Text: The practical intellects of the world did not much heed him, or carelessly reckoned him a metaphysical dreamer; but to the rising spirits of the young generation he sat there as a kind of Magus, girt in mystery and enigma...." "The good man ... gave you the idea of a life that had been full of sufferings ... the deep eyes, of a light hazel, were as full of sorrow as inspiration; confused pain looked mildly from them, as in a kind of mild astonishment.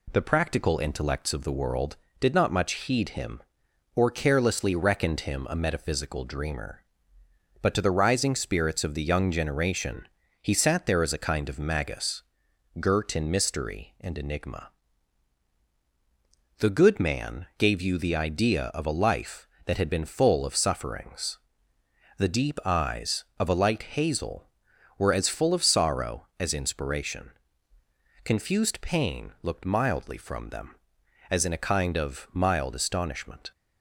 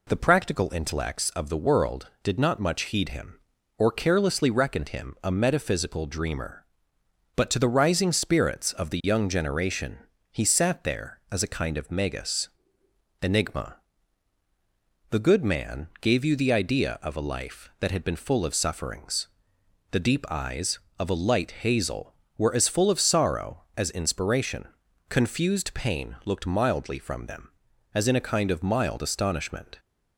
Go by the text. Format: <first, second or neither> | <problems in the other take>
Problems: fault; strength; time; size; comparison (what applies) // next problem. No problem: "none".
first | pauses between "generation" and "he"; slight; at 9.9 s; 0.30 s long; slight in the first // skips "girt in mystery and"; at 12.8 s